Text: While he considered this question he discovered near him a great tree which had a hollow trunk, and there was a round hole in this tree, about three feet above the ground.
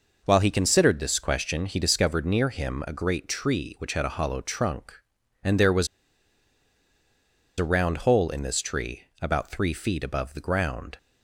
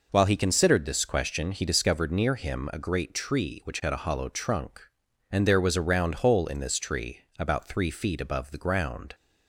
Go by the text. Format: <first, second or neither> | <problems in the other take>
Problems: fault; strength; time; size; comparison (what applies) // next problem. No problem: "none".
second | pauses between "was" and "a"; strong; at 5.8 s; 1.7 s long